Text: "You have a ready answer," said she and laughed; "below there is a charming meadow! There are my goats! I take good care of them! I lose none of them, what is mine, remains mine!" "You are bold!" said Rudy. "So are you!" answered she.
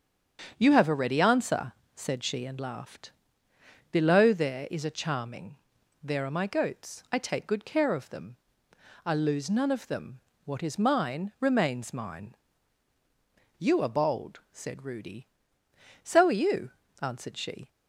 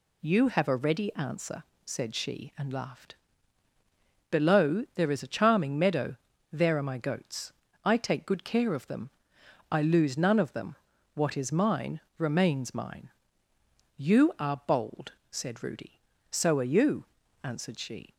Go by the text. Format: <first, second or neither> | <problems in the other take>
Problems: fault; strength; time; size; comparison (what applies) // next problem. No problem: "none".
second | starts louder than the rest; strong; until 1.5 s; 7.5 dB // skips "meadow"; at 5.7 s